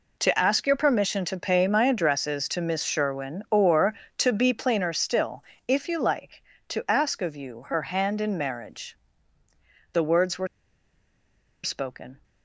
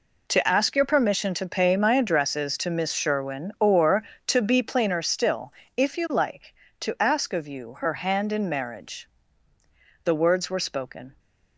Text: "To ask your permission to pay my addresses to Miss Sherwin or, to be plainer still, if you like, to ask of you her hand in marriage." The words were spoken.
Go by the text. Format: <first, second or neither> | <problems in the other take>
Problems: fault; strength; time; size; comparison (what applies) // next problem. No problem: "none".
second | pauses between "were" and "spoken"; at 10.4 s; 1.1 s long